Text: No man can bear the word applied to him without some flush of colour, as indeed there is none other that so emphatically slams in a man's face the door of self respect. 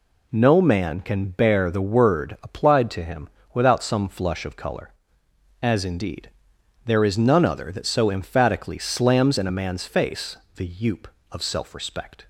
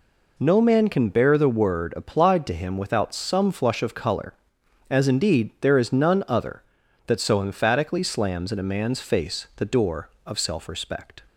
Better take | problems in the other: second | pauses between "him" and "without"; slight; at 3.2 s; 0.24 s long // pauses between "indeed" and "there"; noticeable; at 6.2 s; 0.56 s long // pauses between "face" and "the"; slight; at 10.3 s; 0.20 s long // says "youp" for "door"; at 10.6 s

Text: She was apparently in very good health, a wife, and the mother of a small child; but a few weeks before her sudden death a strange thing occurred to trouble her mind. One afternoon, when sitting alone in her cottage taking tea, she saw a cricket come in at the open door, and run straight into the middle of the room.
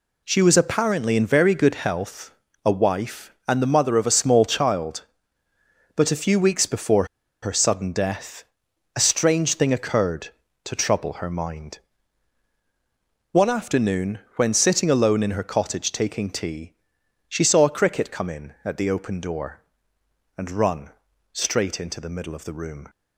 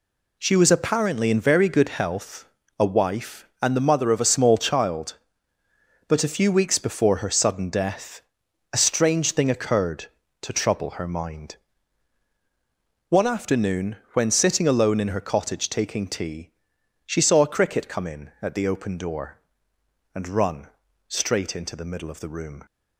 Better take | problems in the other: second | pauses between "before" and "her"; at 7.0 s; 0.37 s long // pauses between "death" and "a"; noticeable; at 8.4 s; 0.52 s long; noticeable in the second // pauses between "run" and "straight"; at 20.8 s; 0.42 s long; also in the second

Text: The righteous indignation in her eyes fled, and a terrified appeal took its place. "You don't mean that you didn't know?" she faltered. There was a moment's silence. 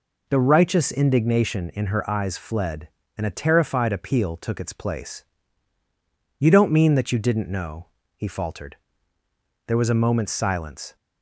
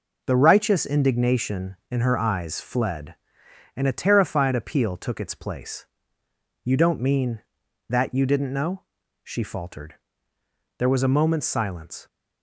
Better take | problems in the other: second | says "he" for "she"; at 8.1 s

